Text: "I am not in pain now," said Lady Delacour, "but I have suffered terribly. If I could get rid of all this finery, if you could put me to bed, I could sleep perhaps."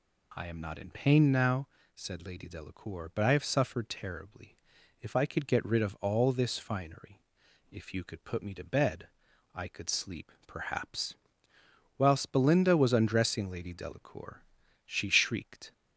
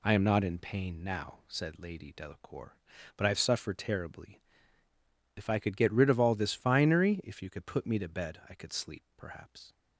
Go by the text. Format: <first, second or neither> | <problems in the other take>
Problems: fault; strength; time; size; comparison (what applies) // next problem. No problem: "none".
second | goes on to say "Whilst Belinda was undressing Lady Delacour she shrieked"; strong; from 11.9 s on; 3.7 s long